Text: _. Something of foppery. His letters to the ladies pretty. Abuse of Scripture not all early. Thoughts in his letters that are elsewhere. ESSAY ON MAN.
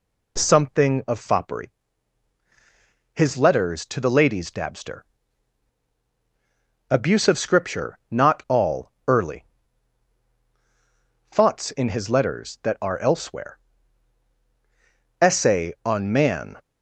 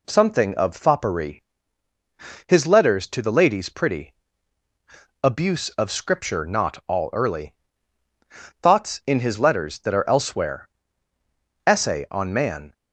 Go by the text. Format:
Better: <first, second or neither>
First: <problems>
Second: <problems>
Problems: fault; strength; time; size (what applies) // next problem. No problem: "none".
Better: second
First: says "dabster" for "pretty"; at 4.5 s // pauses between "all" and "early"; slight; at 8.9 s; 0.16 s long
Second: none